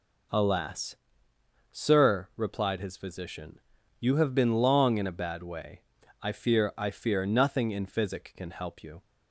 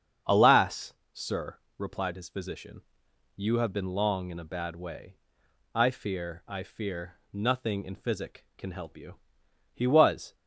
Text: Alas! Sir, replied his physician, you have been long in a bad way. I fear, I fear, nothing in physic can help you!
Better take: first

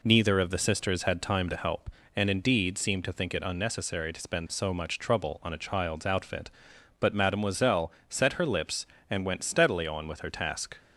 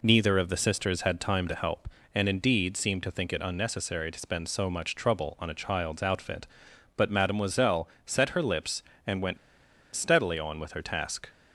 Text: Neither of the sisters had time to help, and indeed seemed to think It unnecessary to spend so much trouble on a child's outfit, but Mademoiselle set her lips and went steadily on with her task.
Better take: first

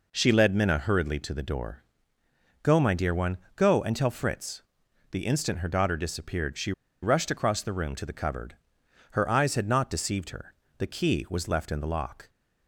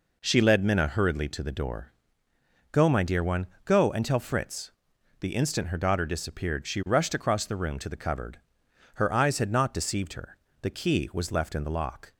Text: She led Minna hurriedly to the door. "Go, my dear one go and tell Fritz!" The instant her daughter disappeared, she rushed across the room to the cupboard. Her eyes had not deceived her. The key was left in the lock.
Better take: second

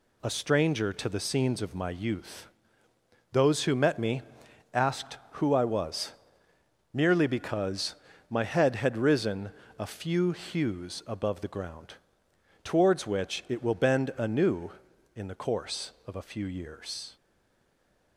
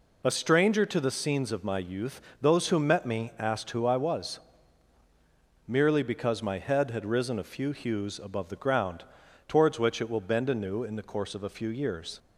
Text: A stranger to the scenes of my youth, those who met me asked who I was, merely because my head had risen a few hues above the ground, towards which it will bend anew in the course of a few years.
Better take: second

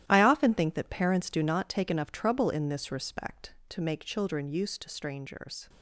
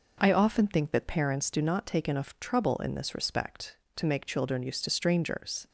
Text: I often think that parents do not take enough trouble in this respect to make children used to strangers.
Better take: second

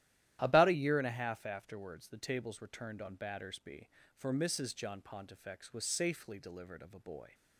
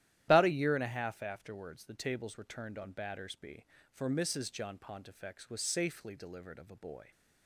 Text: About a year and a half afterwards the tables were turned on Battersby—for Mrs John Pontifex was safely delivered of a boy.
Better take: first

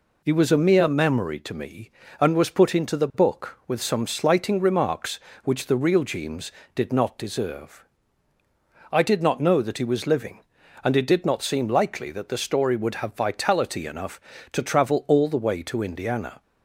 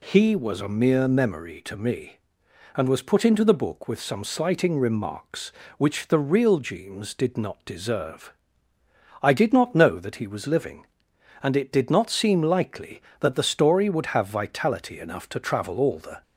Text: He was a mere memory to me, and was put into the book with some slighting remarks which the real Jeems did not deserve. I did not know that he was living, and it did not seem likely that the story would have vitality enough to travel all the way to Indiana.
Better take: first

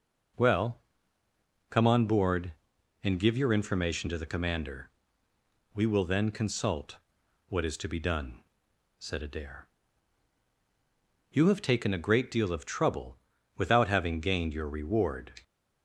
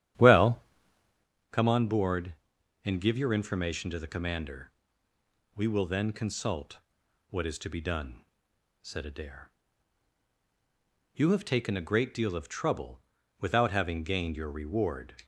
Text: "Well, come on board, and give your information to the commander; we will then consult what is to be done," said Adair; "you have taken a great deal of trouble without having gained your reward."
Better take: first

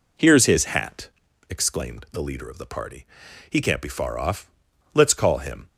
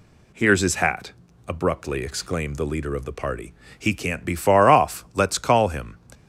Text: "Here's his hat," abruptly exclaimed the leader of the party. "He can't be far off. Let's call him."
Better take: second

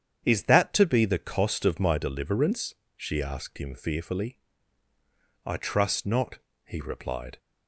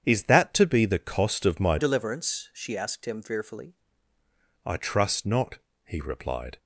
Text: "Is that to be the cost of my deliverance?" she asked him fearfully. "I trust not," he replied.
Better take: first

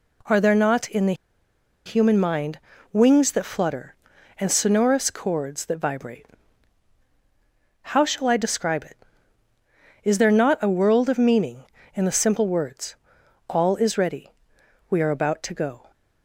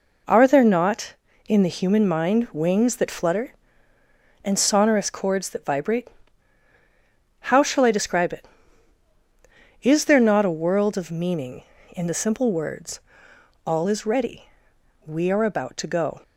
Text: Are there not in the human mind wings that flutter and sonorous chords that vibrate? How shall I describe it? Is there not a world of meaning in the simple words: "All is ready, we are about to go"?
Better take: second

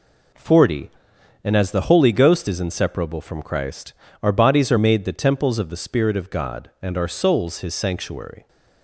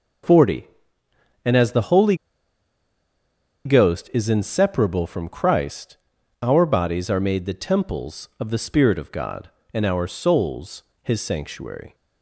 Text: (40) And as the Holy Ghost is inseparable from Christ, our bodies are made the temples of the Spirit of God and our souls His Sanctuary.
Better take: first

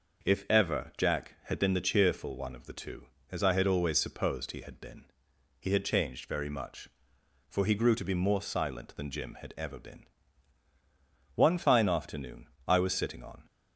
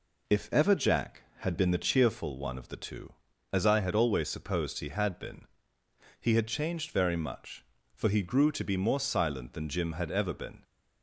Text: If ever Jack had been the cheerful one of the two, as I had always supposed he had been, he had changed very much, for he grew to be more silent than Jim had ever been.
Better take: second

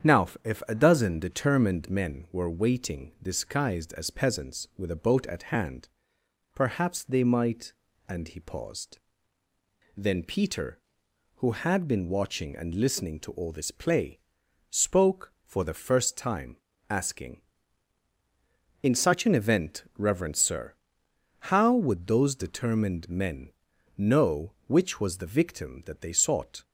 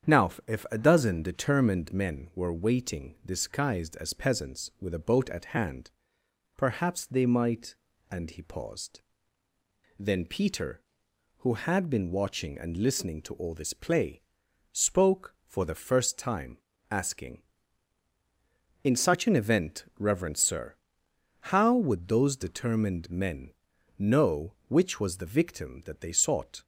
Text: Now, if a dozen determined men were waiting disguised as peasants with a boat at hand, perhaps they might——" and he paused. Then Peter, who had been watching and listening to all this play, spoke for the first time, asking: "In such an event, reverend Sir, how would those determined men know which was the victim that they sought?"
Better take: neither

